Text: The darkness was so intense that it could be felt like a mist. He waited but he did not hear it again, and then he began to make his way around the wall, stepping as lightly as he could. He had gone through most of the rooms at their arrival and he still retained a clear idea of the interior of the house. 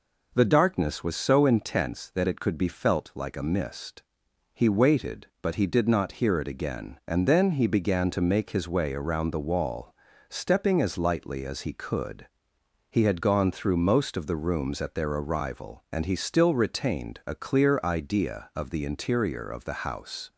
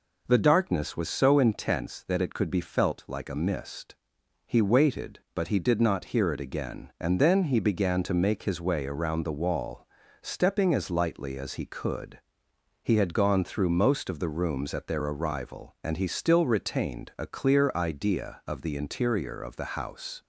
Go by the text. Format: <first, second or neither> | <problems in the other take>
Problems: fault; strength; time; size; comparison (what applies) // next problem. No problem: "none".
neither | none